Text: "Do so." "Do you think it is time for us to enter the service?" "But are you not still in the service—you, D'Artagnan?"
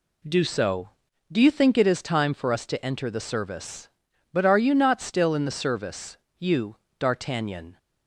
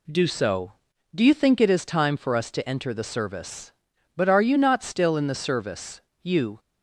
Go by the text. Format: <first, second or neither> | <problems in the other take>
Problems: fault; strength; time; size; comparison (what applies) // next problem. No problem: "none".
first | stops before "D'Artagnan"; at 6.5 s